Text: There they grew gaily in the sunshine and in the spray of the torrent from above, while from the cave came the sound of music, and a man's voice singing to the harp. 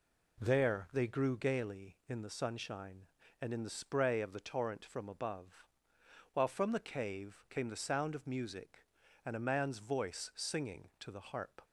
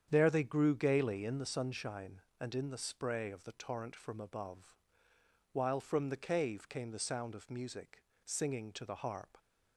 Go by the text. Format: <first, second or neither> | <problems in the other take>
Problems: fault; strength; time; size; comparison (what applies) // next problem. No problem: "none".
first | starts louder than the rest; strong; until 1.1 s; 8.5 dB // skips "and a man's voice"; at 8.1 s